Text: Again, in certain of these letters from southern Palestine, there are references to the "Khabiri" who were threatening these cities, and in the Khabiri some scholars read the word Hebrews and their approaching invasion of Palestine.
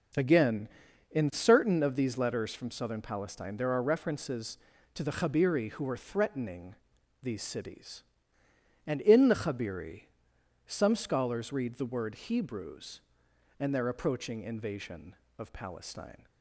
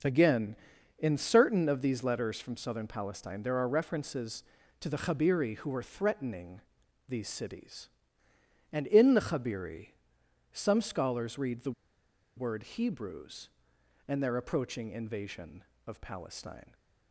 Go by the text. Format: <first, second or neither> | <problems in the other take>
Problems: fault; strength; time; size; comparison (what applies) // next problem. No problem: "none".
first | pauses between "threatening" and "these"; noticeable; at 6.6 s; 0.46 s long; noticeable in the first // pauses between "Khabiri" and "some"; noticeable; at 9.8 s; 0.64 s long; noticeable in the first // pauses between "the" and "word"; noticeable; at 11.7 s; 0.65 s long